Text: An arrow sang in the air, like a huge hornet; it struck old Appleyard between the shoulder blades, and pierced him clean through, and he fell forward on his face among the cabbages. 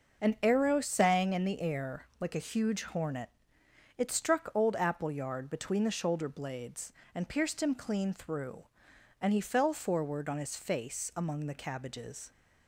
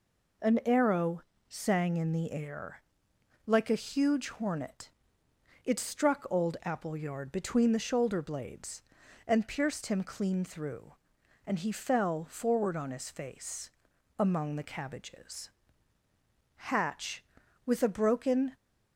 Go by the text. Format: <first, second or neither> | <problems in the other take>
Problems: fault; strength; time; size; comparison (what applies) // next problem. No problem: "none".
first | pauses between "arrow" and "sang"; slight; at 1.2 s; 0.28 s long // pauses between "face" and "among"; at 13.7 s; 0.44 s long // goes on to say "Hatch with a broken"; strong; from 16.5 s on; 1.9 s long